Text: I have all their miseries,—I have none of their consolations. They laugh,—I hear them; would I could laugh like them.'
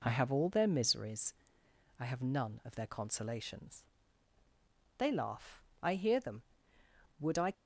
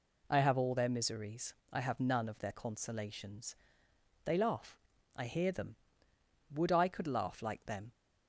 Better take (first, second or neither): second